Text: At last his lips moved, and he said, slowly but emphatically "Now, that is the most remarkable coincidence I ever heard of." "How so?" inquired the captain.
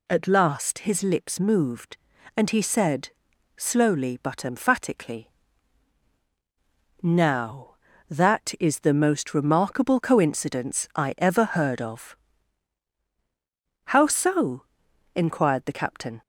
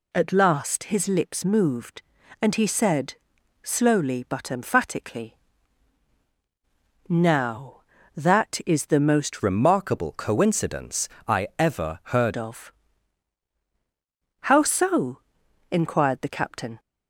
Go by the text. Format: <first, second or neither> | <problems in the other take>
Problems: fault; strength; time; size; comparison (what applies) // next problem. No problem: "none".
first | pauses between "emphatically" and "Now"; strong; at 5.3 s; 1.7 s long; strong in the first // changes voice from "remarkable" to "heard"; from 9.4 to 12.3 s; 2.9 s long // pauses between "coincidence" and "I"; slight; at 11.0 s; 0.22 s long